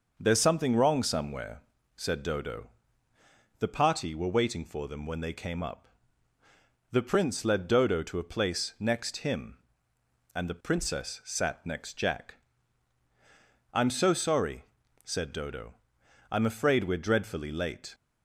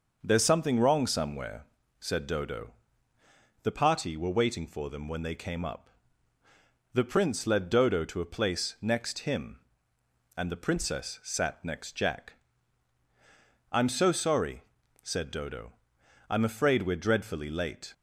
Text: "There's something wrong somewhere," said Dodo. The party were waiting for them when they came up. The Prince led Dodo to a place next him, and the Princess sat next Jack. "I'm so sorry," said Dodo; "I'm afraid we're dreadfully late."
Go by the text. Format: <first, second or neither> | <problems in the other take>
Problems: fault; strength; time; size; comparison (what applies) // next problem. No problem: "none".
neither | starts louder than the rest; the same in both